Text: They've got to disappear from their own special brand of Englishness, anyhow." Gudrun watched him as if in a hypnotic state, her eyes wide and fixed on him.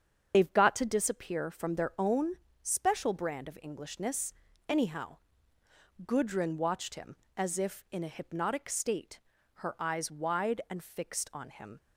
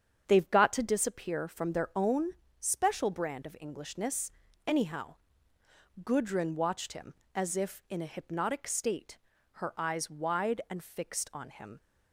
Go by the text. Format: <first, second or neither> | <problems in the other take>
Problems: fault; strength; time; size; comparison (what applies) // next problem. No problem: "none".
second | loses the start of "They've"; at 0.3 s; 50 ms // starts louder than the rest; strong; until 1.3 s; 7 dB; strong in the second // pauses between "own" and "special"; slight; at 2.3 s; 0.28 s long; slight in the second